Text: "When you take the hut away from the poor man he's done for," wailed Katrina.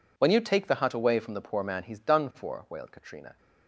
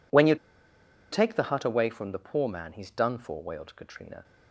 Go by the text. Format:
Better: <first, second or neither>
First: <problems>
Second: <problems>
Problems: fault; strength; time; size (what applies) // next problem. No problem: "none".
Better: first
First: none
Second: pauses between "you" and "take"; noticeable; at 0.3 s; 0.77 s long